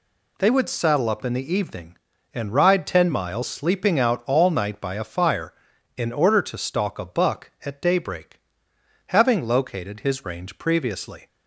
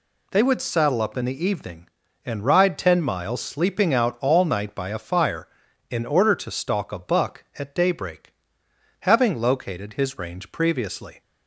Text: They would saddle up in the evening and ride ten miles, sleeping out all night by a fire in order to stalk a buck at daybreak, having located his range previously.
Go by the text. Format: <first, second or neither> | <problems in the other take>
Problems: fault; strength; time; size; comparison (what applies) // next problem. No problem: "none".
neither | none